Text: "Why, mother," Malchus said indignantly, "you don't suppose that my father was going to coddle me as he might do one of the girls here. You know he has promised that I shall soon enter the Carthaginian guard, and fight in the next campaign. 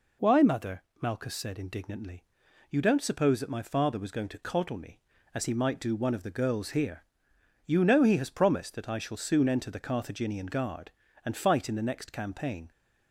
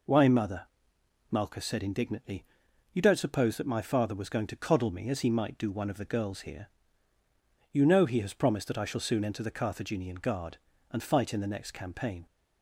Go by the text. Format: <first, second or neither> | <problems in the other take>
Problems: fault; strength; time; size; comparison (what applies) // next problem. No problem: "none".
neither | none